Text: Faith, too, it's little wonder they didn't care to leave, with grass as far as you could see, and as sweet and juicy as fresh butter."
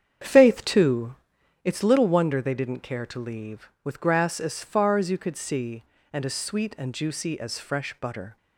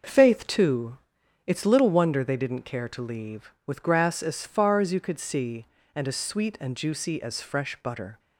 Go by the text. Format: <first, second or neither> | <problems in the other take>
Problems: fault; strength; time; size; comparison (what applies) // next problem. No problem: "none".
second | starts louder than the rest; strong; until 1.6 s; 8 dB